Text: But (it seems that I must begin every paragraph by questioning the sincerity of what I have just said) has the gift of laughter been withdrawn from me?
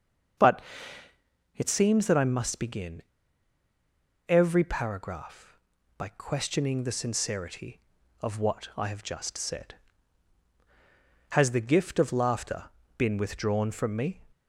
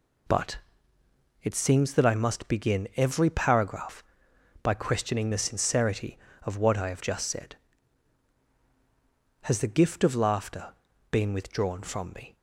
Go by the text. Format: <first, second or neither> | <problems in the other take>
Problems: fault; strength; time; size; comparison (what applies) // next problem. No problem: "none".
second | starts louder than the rest; until 2.3 s; 7 dB // pauses between "begin" and "every"; strong; at 3.0 s; 1.2 s long // pauses between "laughter" and "been"; slight; at 12.6 s; 0.34 s long; also in the second